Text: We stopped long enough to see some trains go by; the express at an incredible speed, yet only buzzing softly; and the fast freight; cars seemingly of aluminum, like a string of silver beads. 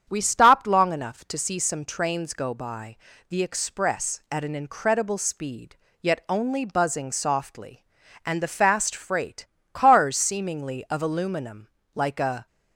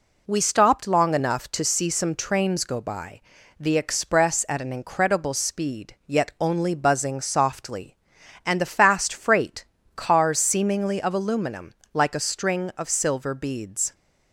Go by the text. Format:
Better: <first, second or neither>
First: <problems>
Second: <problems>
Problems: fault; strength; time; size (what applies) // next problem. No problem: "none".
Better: second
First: starts louder than the rest; strong; until 1.1 s; 8 dB // stops before "string of silver beads"; at 12.4 s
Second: none